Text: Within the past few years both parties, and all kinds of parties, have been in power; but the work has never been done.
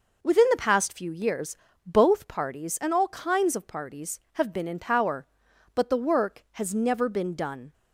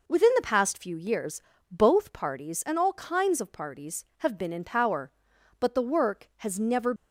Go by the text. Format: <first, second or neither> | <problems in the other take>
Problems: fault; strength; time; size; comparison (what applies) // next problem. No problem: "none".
first | pauses between "years" and "both"; slight; at 1.4 s; 0.30 s long; slight in the first // stops before "been done"; at 6.9 s